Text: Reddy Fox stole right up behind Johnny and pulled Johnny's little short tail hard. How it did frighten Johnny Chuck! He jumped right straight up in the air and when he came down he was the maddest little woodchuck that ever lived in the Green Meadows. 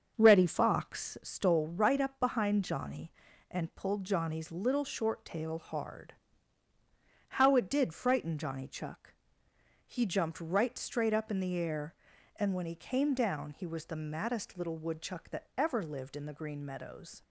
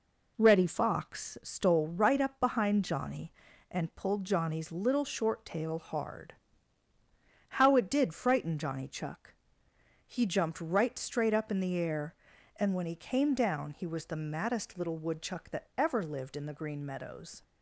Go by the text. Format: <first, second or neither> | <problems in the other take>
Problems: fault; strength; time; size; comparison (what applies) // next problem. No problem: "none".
second | starts louder than the rest; until 1.4 s; 7 dB